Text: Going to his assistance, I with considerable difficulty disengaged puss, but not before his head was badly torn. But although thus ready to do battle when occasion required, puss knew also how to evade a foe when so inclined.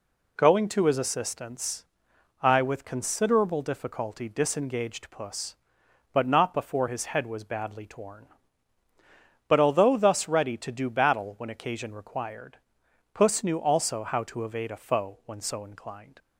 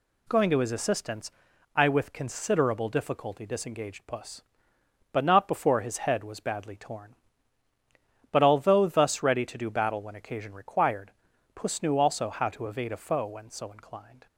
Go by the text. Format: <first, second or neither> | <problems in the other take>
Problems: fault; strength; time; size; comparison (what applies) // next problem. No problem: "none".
neither | none